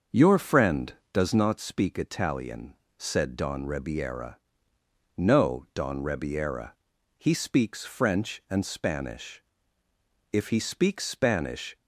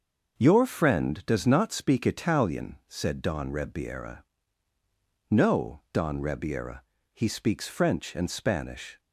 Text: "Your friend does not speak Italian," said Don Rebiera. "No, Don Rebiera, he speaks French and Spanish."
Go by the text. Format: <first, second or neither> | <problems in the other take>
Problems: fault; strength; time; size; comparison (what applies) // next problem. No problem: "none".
second | starts louder than the rest; until 1.3 s; 6.5 dB; noticeable in the second // goes on to say "If he speaks Spanish"; from 10.3 s on; 1.4 s long